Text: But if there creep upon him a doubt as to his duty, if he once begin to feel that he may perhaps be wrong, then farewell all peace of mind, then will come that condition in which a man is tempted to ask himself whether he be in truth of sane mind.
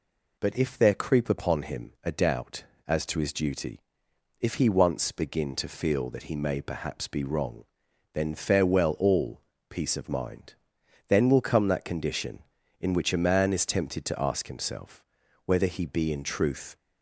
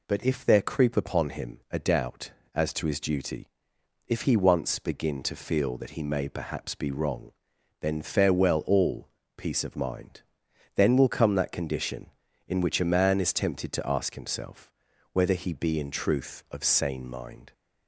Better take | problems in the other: second | pauses between "all" and "peace"; slight; at 9.4 s; 0.28 s long; slight in the second // pauses between "himself" and "whether"; at 15.0 s; 0.42 s long; also in the second // stops before "of sane mind"; at 16.7 s

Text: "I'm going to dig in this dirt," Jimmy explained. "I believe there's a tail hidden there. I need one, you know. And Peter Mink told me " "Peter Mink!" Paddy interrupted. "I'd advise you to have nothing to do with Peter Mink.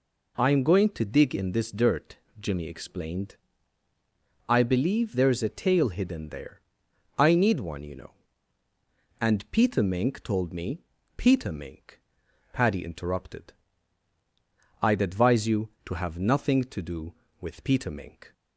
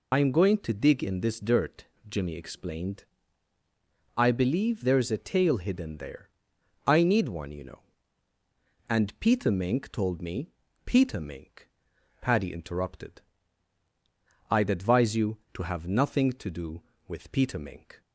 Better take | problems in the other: first | loses the start of "I'm"; at 0.1 s; 70 ms

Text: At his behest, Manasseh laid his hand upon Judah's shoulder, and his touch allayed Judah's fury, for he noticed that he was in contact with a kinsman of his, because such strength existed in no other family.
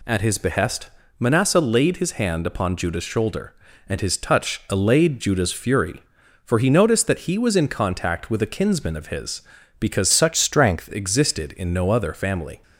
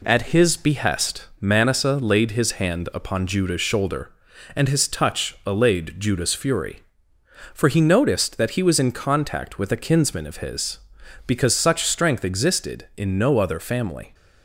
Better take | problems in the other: second | changes voice from "such" to "strength"; from 10.1 to 10.8 s; 0.7 s long

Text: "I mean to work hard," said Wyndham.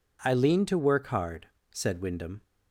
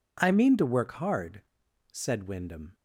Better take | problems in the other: second | says "lean" for "mean"; at 0.3 s

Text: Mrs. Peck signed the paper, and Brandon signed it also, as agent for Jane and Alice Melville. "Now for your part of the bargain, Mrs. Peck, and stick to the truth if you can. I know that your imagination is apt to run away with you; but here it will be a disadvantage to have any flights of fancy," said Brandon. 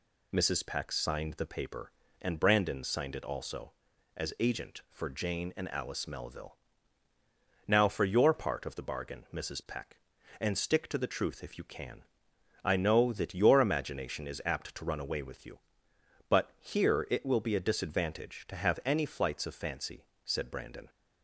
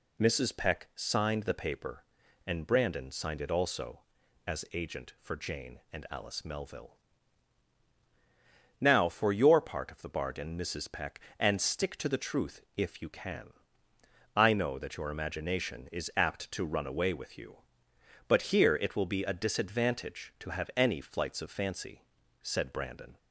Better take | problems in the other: neither | none

